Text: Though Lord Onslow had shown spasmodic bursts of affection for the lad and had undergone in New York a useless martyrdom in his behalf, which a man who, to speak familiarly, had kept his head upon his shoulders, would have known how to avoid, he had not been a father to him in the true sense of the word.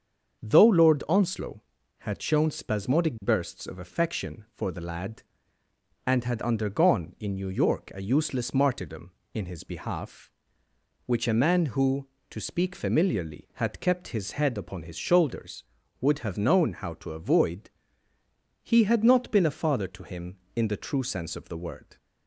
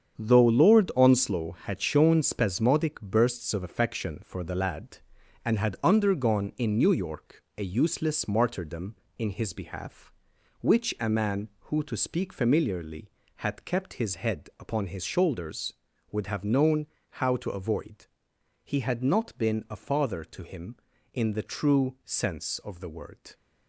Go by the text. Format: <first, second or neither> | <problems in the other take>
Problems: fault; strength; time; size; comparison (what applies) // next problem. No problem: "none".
first | gets quieter; strong; throughout; 8.5 dB // starts louder than the rest; strong; until 1.2 s; 8 dB; also in the first // pauses between "York" and "a"; slight; at 7.4 s; 0.16 s long // pauses between "known" and "how"; slight; at 16.8 s; 0.32 s long